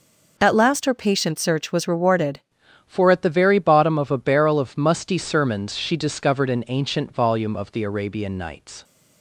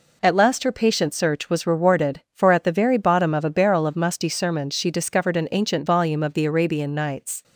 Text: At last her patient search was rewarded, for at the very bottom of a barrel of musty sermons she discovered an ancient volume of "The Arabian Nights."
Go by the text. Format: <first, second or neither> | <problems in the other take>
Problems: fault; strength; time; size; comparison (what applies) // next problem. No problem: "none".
second | changes voice at "for"; from 2.8 s on; 6.0 s long